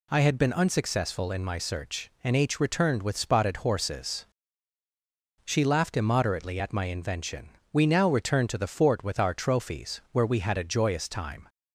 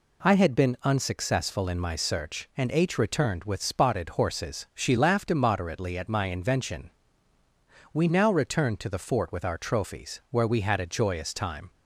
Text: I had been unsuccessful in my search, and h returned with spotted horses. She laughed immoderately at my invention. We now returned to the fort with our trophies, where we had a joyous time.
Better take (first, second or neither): neither